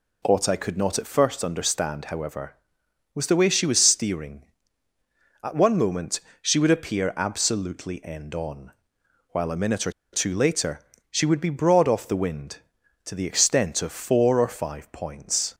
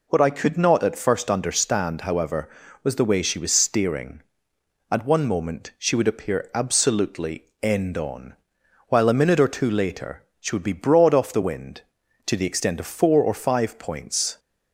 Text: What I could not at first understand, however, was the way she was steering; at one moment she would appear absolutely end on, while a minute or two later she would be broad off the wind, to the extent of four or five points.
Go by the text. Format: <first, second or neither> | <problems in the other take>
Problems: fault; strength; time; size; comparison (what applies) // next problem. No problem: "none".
second | pauses between "moment" and "she"; slight; at 6.2 s; 0.20 s long // pauses between "or" and "two"; slight; at 9.9 s; 0.22 s long // pauses between "later" and "she"; slight; at 10.8 s; 0.28 s long; slight in the second